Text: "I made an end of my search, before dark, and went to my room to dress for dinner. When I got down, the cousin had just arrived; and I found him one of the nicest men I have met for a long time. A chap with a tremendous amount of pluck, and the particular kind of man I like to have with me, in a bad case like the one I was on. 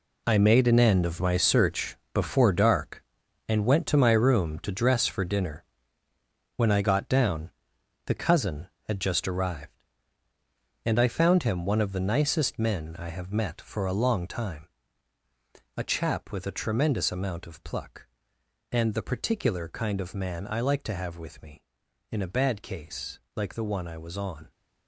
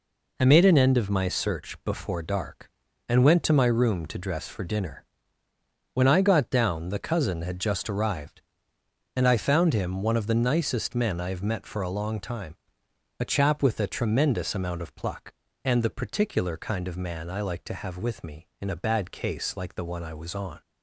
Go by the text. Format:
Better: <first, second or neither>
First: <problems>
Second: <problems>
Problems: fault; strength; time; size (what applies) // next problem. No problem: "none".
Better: second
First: gets quieter; strong; throughout; 10.5 dB // pauses between "case" and "like"; slight; at 23.1 s; 0.16 s long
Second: none